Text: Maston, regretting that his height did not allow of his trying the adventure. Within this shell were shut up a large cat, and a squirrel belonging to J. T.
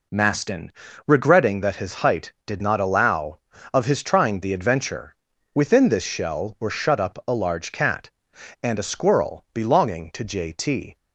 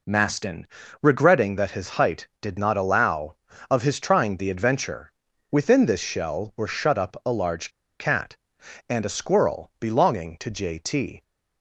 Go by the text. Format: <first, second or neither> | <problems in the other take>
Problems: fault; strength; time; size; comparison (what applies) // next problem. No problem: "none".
first | pauses between "large" and "cat"; slight; at 7.6 s; 0.30 s long